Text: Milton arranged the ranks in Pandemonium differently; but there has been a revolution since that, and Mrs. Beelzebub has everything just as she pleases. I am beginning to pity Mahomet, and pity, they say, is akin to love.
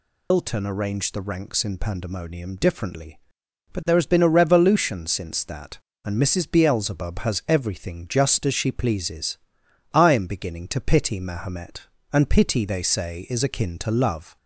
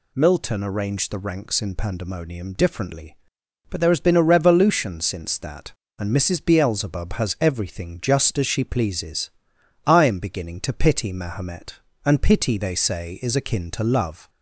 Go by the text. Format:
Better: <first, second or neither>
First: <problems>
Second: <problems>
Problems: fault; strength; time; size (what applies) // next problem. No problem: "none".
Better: second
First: loses the start of "Milton"; at 0.3 s; 130 ms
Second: none